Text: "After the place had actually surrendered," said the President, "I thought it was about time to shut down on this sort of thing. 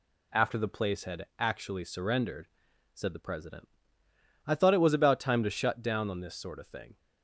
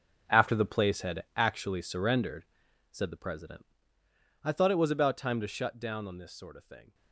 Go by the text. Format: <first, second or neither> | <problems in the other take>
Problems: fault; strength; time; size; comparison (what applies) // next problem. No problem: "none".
first | gets quieter; strong; throughout; 13.5 dB